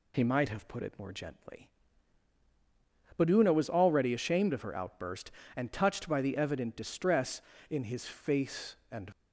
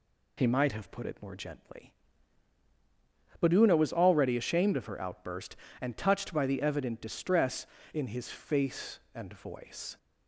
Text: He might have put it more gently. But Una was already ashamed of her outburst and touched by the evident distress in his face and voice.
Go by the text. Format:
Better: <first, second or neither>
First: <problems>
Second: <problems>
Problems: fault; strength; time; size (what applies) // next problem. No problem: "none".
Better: second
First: stops before "voice"; at 9.1 s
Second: none